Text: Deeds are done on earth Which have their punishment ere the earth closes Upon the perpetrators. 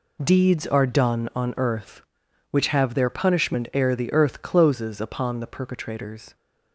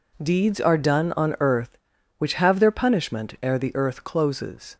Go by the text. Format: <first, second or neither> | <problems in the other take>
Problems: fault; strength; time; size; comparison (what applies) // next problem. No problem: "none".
first | stops before "Upon the perpetrators"; at 4.7 s